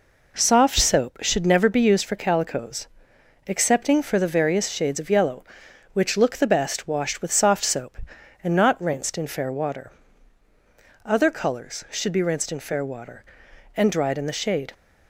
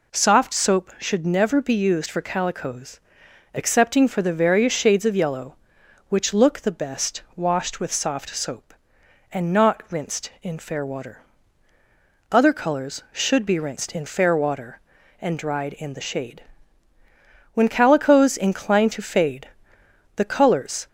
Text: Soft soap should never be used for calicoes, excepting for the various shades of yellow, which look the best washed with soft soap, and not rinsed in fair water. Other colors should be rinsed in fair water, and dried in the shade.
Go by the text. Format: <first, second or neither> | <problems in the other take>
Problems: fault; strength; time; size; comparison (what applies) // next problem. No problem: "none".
first | goes on to say "When calicoes incline to fade the colors"; strong; from 17.5 s on; 3.3 s long